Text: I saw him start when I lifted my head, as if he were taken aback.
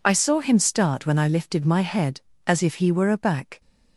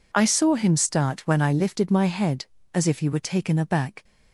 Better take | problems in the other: second | skips "taken"; at 3.1 s

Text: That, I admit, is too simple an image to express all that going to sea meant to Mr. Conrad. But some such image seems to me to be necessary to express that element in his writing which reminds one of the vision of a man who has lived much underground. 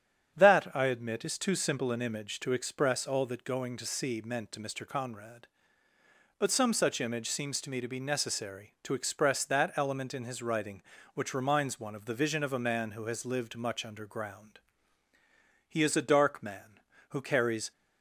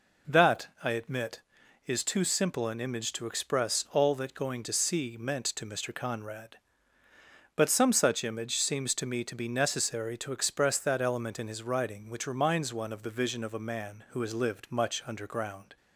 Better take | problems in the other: second | starts louder than the rest; strong; until 1.3 s; 8.5 dB // goes on to say "He is a dark man who carries"; strong; from 15.6 s on; 2.0 s long

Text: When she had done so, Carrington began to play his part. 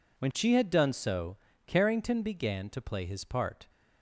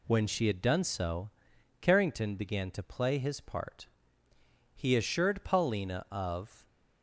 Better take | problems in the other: first | goes on to say "He assured Paulina of"; strong; from 4.7 s on; 1.9 s long

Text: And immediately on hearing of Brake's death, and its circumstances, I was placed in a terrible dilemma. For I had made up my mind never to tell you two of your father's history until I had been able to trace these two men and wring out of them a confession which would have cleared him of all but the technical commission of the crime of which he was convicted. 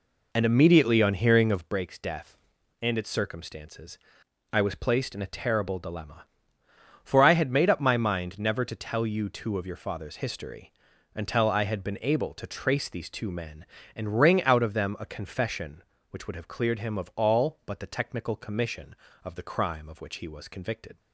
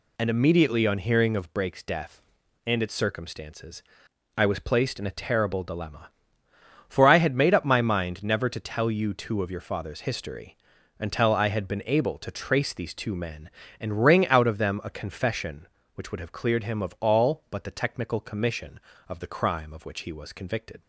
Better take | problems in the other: second | starts louder than the rest; until 1.8 s; 3.5 dB // pauses between "history" and "until"; at 10.7 s; 0.44 s long; also in the second

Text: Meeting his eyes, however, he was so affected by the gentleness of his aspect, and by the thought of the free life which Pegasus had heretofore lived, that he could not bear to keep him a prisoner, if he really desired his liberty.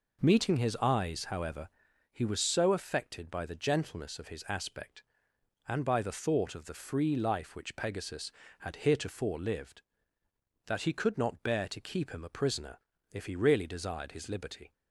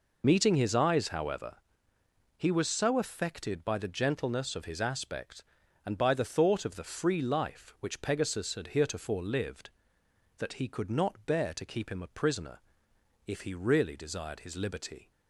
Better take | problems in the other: first | loses the start of "Meeting"; at 0.2 s; 40 ms

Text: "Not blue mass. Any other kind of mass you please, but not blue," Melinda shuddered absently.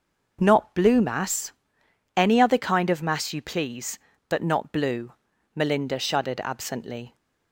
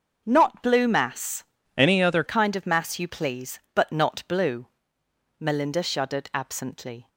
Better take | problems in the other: first | changes voice from "Any" to "other"; from 1.7 to 2.2 s; 0.5 s long

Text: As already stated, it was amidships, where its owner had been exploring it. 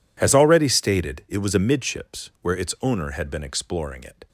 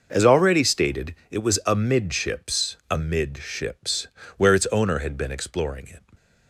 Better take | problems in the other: first | says "amidships" twice; at 2.9 s

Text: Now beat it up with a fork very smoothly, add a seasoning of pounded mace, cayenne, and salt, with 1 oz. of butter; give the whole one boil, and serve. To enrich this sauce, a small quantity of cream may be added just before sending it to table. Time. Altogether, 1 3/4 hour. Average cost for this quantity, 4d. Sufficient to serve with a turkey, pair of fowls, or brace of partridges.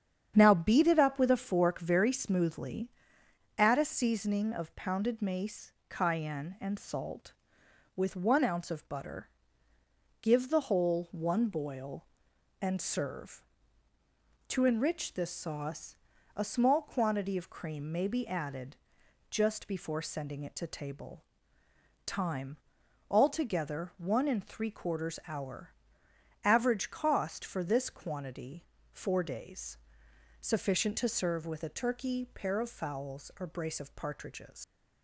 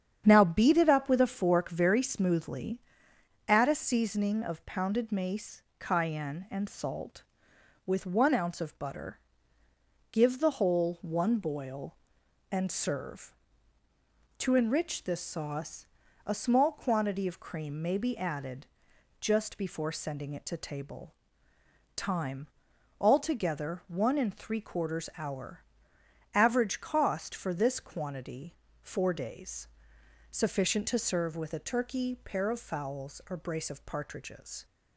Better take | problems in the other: second | starts louder than the rest; strong; until 1.3 s; 8.5 dB; strong in the second // pauses between "added" and "just"; noticeable; at 18.7 s; 0.56 s long; noticeable in the second // leaves "partridges" unfinished; at 34.6 s; 105 ms

